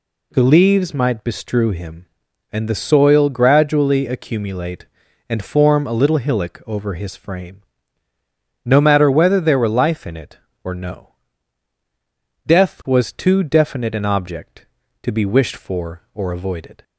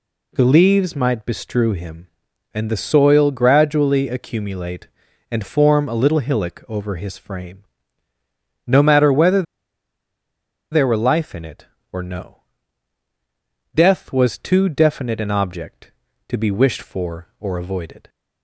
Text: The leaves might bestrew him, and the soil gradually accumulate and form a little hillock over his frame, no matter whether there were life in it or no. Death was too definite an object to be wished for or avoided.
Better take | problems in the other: first | pauses between "whether" and "there"; strong; at 9.4 s; 1.2 s long

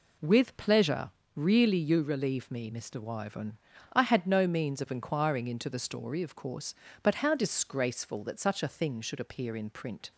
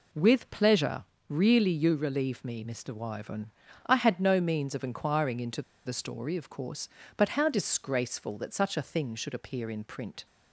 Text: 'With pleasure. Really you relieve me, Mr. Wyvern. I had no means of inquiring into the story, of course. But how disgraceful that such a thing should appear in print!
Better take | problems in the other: first | pauses between "into" and "the"; slight; at 5.6 s; 0.24 s long

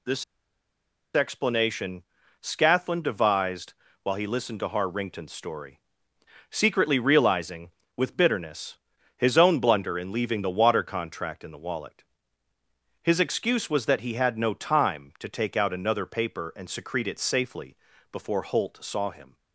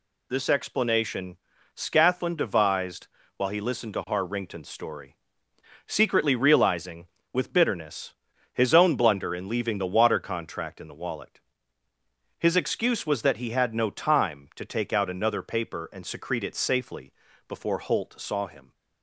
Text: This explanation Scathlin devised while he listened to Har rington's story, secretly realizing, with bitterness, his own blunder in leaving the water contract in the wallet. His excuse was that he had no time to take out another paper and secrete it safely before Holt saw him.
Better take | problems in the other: second | pauses between "This" and "explanation"; noticeable; at 0.2 s; 0.90 s long // pauses between "explanation" and "Scathlin"; at 2.0 s; 0.40 s long; also in the second // pauses between "devised" and "while"; slight; at 3.7 s; 0.28 s long; slight in the second // pauses between "safely" and "before"; slight; at 17.7 s; 0.34 s long; slight in the second

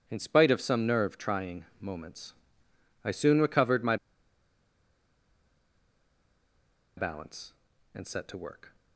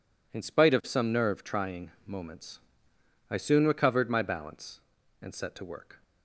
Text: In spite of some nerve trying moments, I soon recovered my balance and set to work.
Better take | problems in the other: second | pauses between "trying" and "moments"; slight; at 1.6 s; 0.16 s long; slight in the second // pauses between "my" and "balance"; strong; at 3.9 s; 3.0 s long

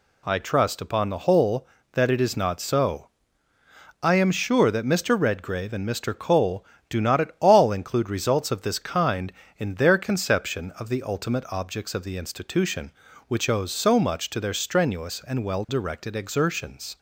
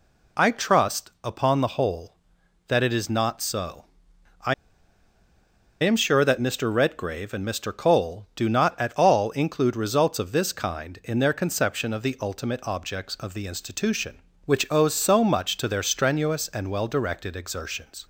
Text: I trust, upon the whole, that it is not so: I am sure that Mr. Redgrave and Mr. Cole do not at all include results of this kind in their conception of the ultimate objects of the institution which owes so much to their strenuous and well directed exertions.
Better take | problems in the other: first | pauses between "I" and "am"; strong; at 4.5 s; 1.2 s long

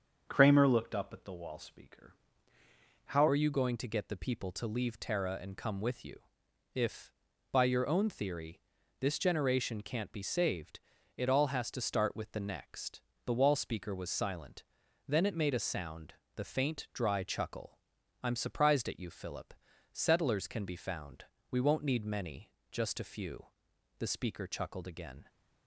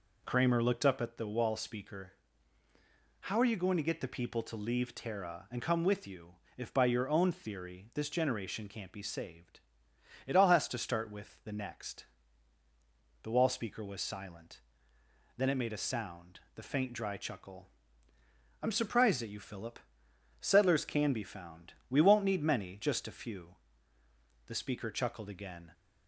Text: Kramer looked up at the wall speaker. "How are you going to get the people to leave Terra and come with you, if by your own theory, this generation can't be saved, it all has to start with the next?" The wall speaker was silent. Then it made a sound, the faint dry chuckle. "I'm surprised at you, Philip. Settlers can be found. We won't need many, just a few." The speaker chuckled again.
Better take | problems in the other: second | starts louder than the rest; until 1.2 s; 6.5 dB // changes voice at "are"; from 3.2 s on; 22.0 s long

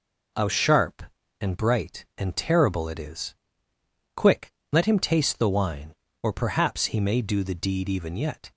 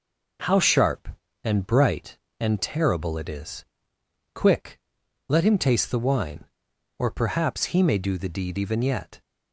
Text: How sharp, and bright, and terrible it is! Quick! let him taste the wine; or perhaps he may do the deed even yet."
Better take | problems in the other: neither | none

